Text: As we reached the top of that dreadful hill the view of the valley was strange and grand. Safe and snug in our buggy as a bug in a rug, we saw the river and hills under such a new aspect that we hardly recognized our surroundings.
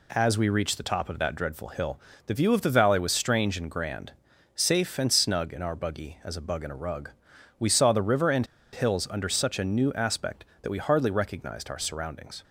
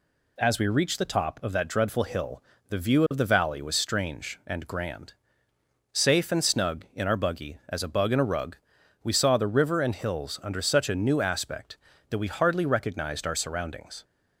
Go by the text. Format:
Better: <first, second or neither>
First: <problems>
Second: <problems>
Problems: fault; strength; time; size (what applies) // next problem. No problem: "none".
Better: second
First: pauses between "hill" and "the"; slight; at 1.9 s; 0.28 s long // pauses between "and" and "hills"; slight; at 8.4 s; 0.28 s long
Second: pauses between "hill" and "the"; slight; at 2.4 s; 0.26 s long